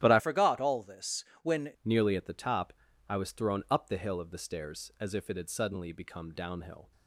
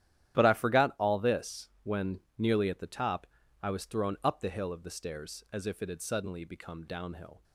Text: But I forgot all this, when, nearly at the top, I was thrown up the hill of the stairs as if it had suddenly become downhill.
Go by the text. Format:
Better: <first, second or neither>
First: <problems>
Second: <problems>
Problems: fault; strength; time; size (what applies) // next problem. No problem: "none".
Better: second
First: starts louder than the rest; strong; until 1.0 s; 13.5 dB // changes voice from "forgot" to "when"; from 0.1 to 1.7 s; 1.6 s long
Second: starts louder than the rest; strong; until 1.4 s; 12 dB